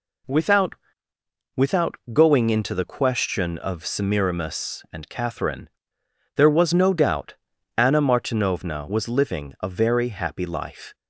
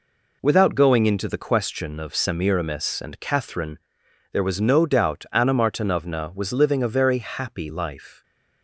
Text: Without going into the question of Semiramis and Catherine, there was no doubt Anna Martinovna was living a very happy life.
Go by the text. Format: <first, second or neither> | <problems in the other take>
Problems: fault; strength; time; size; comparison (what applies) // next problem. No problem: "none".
second | says "Without" twice; at 1.5 s // pauses between "doubt" and "Anna"; at 7.3 s; 0.42 s long